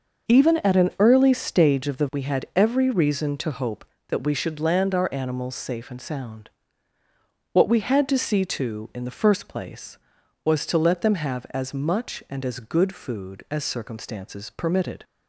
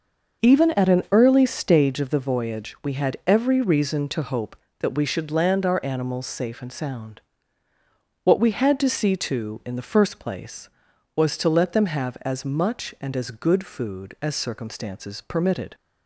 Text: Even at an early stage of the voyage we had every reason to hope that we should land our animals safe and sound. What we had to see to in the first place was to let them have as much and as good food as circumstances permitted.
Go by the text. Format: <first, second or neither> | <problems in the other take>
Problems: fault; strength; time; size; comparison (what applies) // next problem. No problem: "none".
second | starts louder than the rest; noticeable; until 1.3 s; 6 dB // skips "voyage"; at 2.0 s